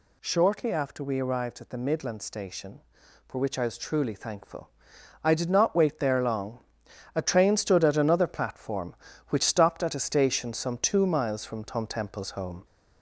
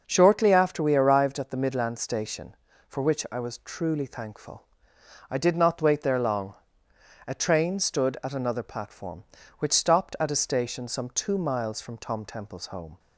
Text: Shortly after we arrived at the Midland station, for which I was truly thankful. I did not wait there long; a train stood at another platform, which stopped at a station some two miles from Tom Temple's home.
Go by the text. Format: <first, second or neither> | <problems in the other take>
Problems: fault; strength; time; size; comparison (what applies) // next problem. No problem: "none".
second | gets louder; slight; throughout; 2.5 dB